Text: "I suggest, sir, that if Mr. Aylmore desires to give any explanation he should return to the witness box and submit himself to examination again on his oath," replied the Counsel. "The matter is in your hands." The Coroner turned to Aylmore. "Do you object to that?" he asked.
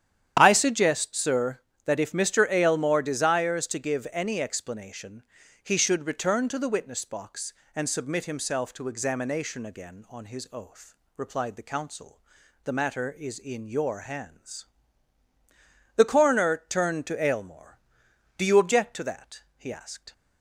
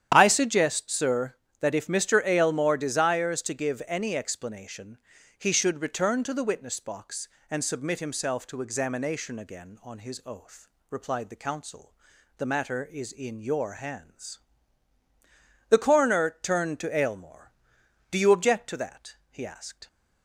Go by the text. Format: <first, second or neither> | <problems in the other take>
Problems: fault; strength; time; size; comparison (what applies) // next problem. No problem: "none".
neither | starts louder than the rest; strong; the same in both // pauses between "explanation" and "he"; the same in both